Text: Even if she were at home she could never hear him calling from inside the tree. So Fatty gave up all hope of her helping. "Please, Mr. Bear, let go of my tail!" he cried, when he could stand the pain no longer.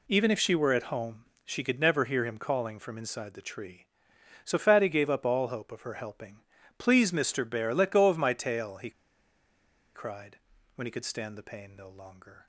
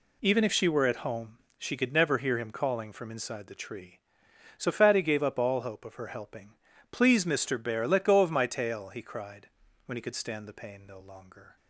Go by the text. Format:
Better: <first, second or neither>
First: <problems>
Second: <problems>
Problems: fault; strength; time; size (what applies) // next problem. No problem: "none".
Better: second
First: pauses between "home" and "she"; slight; at 1.2 s; 0.22 s long // pauses between "he" and "cried"; at 8.9 s; 1.0 s long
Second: pauses between "home" and "she"; slight; at 1.3 s; 0.22 s long